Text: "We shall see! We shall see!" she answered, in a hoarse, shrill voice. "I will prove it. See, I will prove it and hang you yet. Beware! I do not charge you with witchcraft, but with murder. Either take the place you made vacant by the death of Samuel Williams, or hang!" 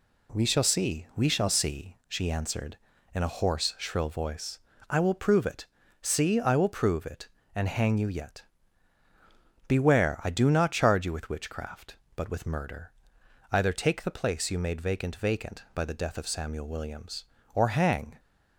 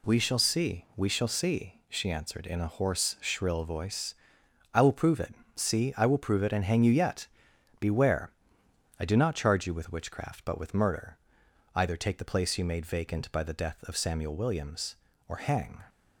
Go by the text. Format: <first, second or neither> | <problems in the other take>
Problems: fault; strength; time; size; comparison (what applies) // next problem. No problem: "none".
second | says "vacant" twice; at 15.1 s